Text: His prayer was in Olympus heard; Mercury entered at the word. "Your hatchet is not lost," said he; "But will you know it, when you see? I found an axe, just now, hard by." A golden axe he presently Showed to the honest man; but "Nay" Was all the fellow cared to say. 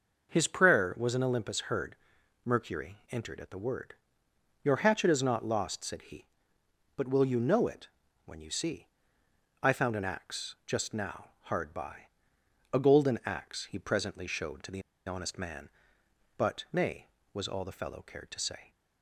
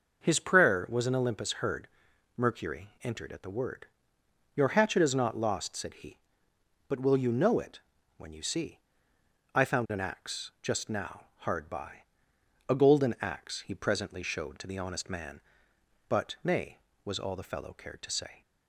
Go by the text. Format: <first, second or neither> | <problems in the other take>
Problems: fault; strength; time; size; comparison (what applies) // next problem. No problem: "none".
second | pauses between "the" and "honest"; slight; at 14.8 s; 0.26 s long